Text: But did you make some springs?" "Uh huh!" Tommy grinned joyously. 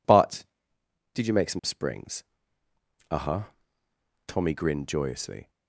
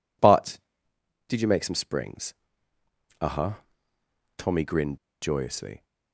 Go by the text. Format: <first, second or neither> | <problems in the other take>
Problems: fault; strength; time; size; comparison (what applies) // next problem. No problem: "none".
first | pauses between "grinned" and "joyously"; slight; at 4.9 s; 0.23 s long